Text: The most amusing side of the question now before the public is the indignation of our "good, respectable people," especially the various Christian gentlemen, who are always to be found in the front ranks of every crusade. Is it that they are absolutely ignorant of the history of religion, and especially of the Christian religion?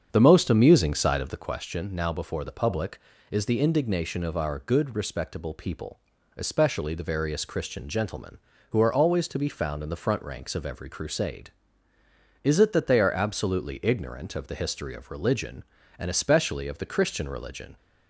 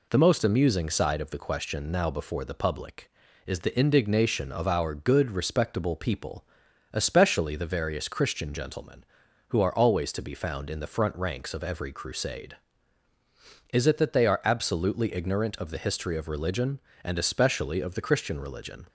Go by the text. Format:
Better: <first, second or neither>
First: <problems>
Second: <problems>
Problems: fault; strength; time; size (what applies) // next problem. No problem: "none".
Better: second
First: starts louder than the rest; strong; until 1.6 s; 7.5 dB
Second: none